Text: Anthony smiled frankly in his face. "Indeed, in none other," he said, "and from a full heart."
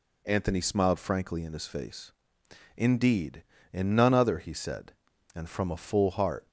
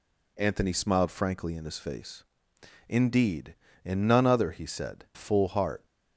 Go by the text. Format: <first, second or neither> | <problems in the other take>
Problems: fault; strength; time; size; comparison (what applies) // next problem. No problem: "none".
first | skips "and from a"; at 5.0 s